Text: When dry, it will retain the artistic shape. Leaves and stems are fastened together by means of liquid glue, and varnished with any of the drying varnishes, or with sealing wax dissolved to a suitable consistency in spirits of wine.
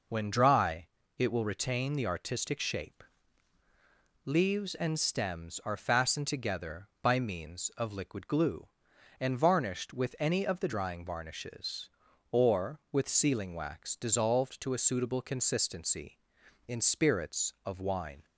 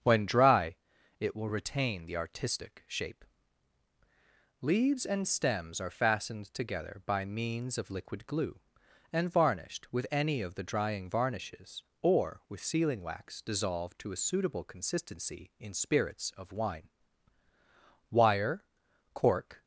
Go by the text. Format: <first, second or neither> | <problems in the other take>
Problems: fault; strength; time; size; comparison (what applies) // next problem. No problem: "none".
first | starts louder than the rest; strong; until 1.4 s; 7.5 dB // goes on to say "Wire cork"; from 18.1 s on; 1.5 s long